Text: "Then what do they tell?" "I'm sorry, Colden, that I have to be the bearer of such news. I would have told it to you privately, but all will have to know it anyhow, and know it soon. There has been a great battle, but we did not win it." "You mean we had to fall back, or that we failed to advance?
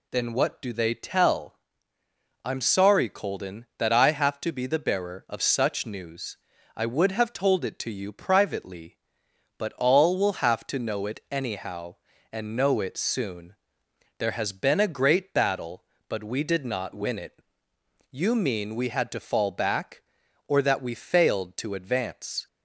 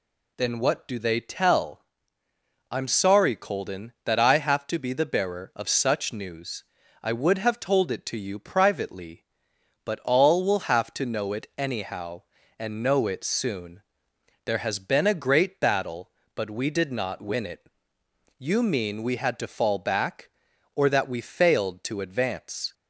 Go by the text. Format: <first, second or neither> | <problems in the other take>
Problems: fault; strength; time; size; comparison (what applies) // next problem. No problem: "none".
neither | none